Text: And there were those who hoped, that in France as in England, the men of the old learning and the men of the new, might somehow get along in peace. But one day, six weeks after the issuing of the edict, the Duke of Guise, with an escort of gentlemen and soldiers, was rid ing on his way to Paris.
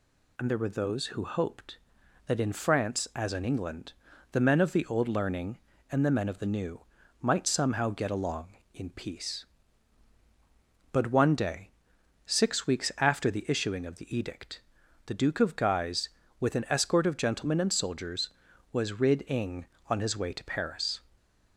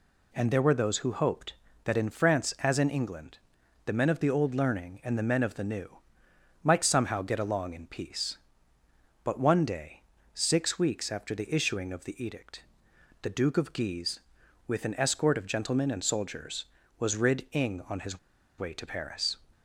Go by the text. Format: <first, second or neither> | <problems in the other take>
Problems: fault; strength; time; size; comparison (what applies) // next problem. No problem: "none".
first | pauses between "his" and "way"; at 18.1 s; 0.40 s long